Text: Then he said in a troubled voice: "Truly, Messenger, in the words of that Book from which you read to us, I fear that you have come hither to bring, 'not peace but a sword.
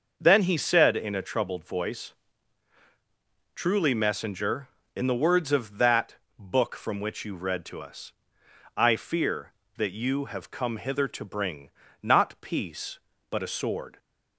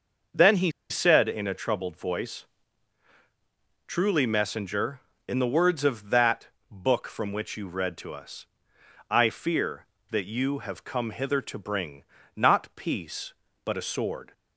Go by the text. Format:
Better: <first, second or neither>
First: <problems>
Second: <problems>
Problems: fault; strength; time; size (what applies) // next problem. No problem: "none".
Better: first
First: starts louder than the rest; noticeable; until 1.1 s; 6 dB // pauses between "that" and "Book"; slight; at 6.1 s; 0.24 s long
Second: starts louder than the rest; noticeable; until 1.5 s; 6 dB // pauses between "he" and "said"; slight; at 0.7 s; 0.19 s long // pauses between "that" and "Book"; slight; at 6.4 s; 0.24 s long